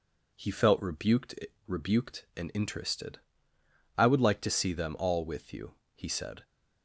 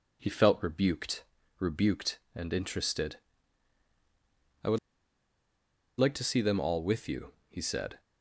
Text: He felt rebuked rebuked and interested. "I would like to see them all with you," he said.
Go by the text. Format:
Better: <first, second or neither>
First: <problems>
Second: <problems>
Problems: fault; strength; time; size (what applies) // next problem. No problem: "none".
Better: first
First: pauses between "rebuked" and "rebuked"; slight; at 1.3 s; 0.32 s long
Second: pauses between "rebuked" and "rebuked"; slight; at 1.2 s; 0.34 s long // pauses between "would" and "like"; at 4.7 s; 1.2 s long